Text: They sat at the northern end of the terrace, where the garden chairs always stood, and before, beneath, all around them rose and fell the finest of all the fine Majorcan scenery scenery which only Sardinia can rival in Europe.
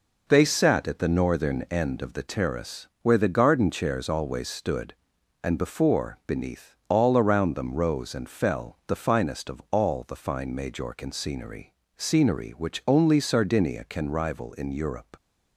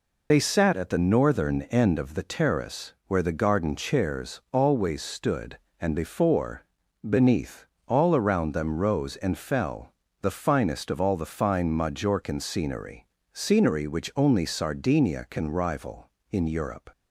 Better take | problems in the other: first | loses the start of "They"; at 0.3 s; 45 ms // pauses between "fell" and "the"; slight; at 9.9 s; 0.30 s long // pauses between "scenery" and "scenery"; slight; at 13.0 s; 0.28 s long; slight in the first

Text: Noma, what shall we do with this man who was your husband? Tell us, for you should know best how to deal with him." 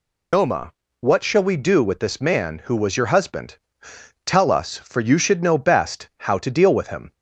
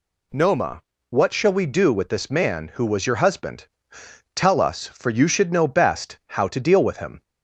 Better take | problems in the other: second | loses the start of "Noma"; at 0.3 s; 105 ms

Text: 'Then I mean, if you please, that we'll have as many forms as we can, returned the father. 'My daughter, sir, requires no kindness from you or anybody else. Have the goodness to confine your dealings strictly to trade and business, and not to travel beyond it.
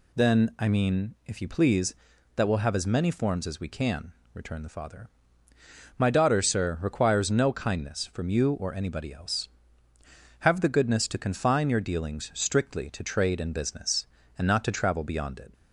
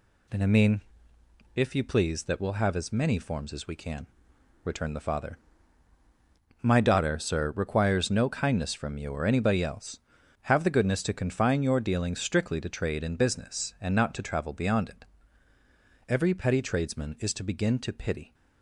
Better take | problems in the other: first | goes on to say "Every petty tradesman is to begin to pity"; strong; from 16.0 s on; 2.2 s long

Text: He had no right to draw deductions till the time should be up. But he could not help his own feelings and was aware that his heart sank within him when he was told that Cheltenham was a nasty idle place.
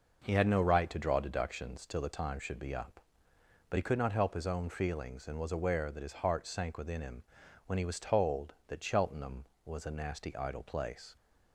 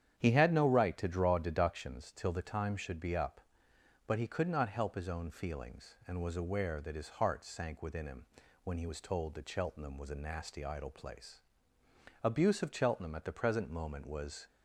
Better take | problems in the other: first | starts louder than the rest; strong; until 1.1 s; 9 dB // pauses between "him" and "when"; at 8.2 s; 0.38 s long; noticeable in the first // goes on to say "Abuse of Cheltenham at the present moment was"; strong; from 12.2 s on; 2.2 s long

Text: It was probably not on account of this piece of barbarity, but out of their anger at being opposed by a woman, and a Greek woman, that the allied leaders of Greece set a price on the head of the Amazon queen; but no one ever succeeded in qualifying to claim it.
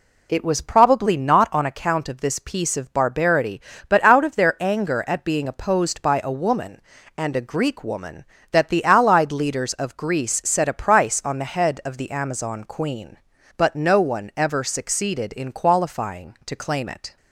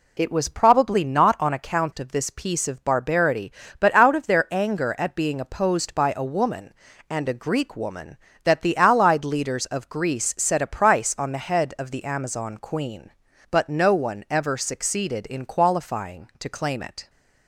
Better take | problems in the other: neither | none

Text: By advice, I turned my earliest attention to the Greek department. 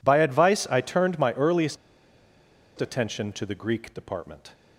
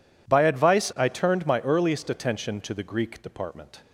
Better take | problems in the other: second | pauses between "earliest" and "attention"; at 1.7 s; 1.0 s long

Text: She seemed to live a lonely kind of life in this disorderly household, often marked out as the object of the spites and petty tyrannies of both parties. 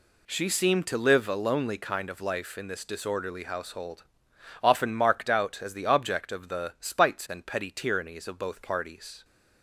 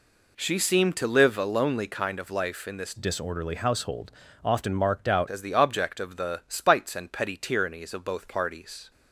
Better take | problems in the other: first | changes voice from "disorderly" to "out"; from 2.9 to 5.2 s; 2.3 s long

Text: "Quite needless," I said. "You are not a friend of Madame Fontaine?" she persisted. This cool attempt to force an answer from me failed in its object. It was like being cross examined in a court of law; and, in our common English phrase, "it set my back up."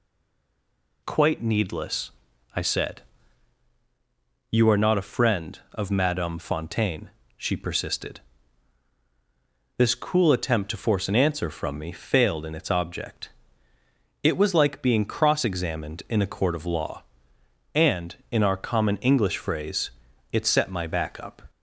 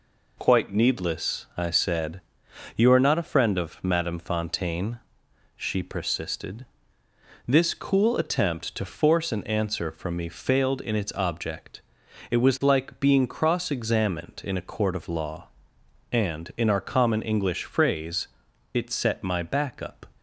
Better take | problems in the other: second | stays silent before the first word; until 1.0 s; 1.0 s long

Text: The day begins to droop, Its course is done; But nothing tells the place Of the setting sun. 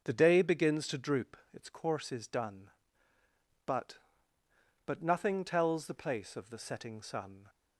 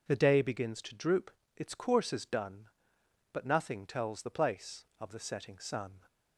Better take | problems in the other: second | starts louder than the rest; until 1.0 s; 6.5 dB // says "But" twice; at 4.8 s

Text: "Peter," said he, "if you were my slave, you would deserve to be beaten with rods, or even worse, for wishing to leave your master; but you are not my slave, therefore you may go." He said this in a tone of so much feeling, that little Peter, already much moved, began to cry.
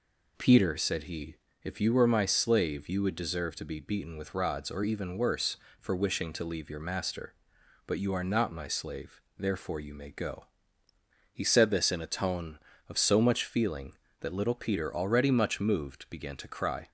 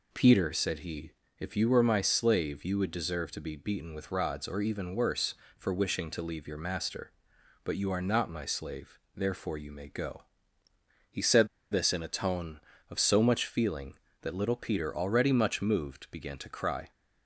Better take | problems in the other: first | pauses between "said" and "this"; slight; at 11.4 s; 0.24 s long

